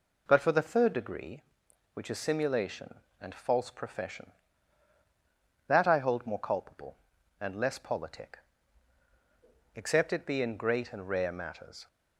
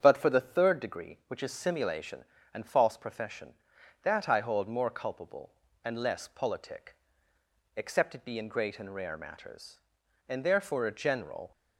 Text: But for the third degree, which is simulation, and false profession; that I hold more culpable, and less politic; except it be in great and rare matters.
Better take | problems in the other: first | starts louder than the rest; strong; until 1.0 s; 7.5 dB // goes on to say "And therefore a general"; noticeable; from 10.2 s on; 1.2 s long

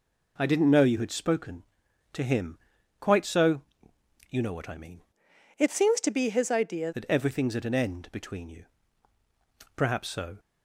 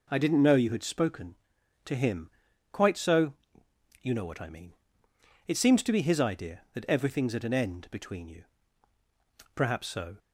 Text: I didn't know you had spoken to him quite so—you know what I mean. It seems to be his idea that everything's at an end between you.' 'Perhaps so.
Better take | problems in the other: second | pauses between "him" and "quite"; at 2.5 s; 0.42 s long; also in the second // changes voice from "It" to "idea"; from 5.5 to 6.9 s; 1.4 s long

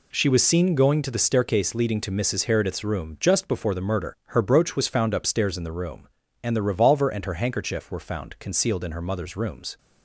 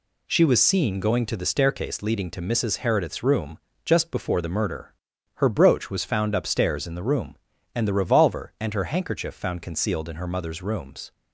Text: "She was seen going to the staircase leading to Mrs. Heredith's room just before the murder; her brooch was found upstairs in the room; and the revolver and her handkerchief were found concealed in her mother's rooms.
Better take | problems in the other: first | pauses between "room" and "just"; slight; at 3.6 s; 0.24 s long // skips "were"; at 9.3 s

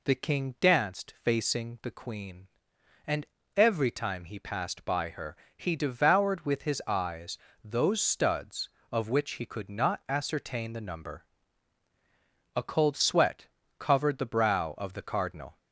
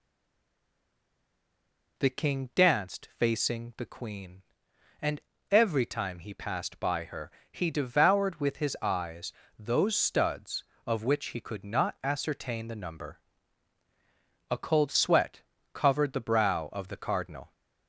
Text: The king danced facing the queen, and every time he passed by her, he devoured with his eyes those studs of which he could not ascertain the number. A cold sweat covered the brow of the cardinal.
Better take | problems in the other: first | stays silent before the first word; noticeable; until 1.9 s; 1.9 s long // pauses between "and" and "every"; slight; at 5.1 s; 0.32 s long; slight in the first // pauses between "eyes" and "those"; slight; at 9.3 s; 0.26 s long; slight in the first // pauses between "sweat" and "covered"; slight; at 15.4 s; 0.32 s long; slight in the first

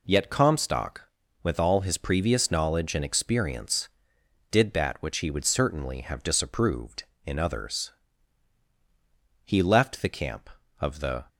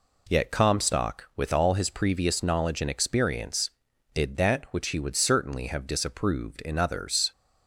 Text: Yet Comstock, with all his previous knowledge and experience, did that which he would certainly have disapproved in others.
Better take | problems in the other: second | goes on to say "He left the camp of the"; strong; from 9.4 s on; 1.8 s long

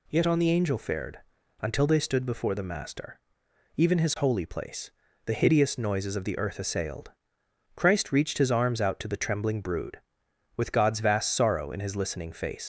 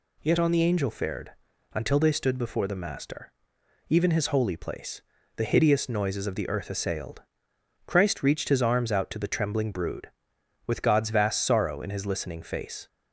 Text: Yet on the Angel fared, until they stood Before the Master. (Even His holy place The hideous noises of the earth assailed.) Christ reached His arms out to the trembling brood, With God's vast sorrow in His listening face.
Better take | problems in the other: second | pauses between "place" and "The"; slight; at 4.8 s; 0.36 s long; slight in the second // leaves "face" unfinished; at 12.6 s; 90 ms

